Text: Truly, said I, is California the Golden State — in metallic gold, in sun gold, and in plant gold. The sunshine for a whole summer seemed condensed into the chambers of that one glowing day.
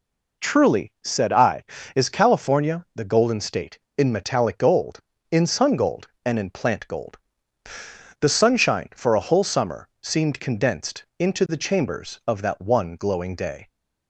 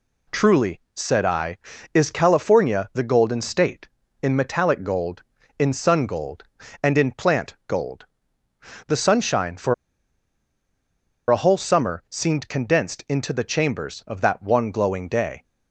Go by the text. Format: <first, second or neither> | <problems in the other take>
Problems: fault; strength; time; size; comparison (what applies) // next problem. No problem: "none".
first | pauses between "for" and "a"; strong; at 9.7 s; 1.5 s long